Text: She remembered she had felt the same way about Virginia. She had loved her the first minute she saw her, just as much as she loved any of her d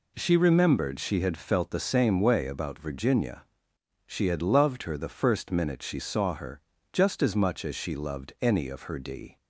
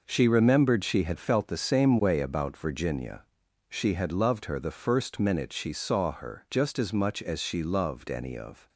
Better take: first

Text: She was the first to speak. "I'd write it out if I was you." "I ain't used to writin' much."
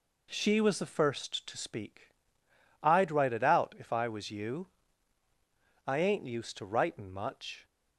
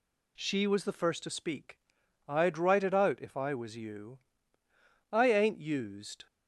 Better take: first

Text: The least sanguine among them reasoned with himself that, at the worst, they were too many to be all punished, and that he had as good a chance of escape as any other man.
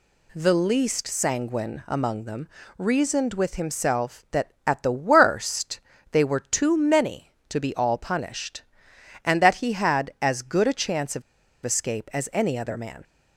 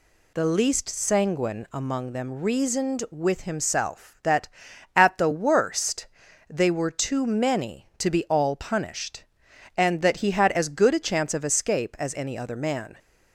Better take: second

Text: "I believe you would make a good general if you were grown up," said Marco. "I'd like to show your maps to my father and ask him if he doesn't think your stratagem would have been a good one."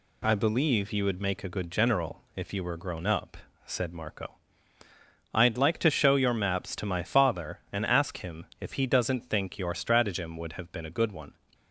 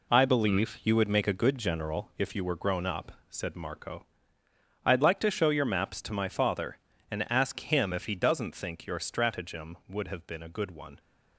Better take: first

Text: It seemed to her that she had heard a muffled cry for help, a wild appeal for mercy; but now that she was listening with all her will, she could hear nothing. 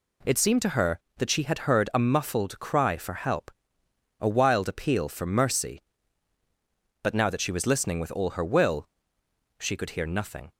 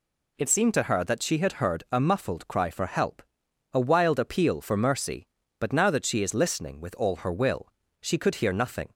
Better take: first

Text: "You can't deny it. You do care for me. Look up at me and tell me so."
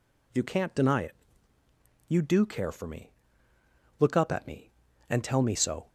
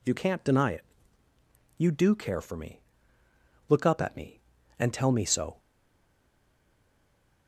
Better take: first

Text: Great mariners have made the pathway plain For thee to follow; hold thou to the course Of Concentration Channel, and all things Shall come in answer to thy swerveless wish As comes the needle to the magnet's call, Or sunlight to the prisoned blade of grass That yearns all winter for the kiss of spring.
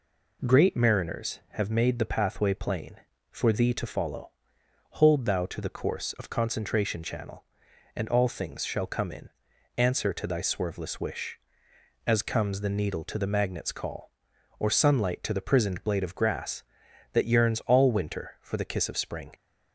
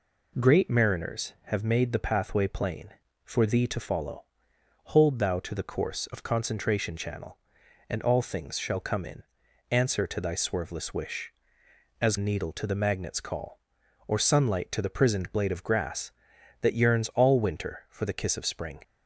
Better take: first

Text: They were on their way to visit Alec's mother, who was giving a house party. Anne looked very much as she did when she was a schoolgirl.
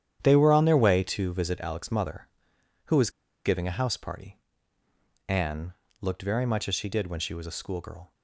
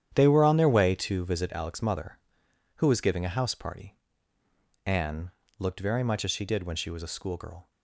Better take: second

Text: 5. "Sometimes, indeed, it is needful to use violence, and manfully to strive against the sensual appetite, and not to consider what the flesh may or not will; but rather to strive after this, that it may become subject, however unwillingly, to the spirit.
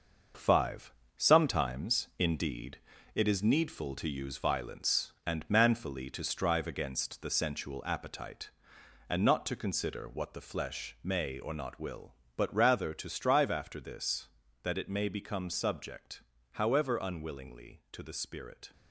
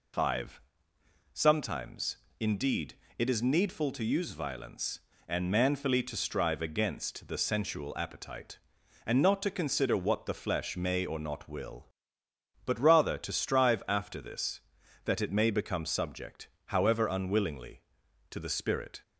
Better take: second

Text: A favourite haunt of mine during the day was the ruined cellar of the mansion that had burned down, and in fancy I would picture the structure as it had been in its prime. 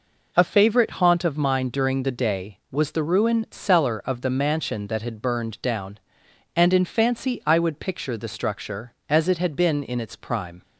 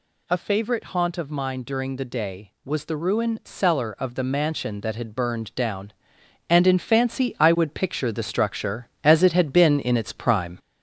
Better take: first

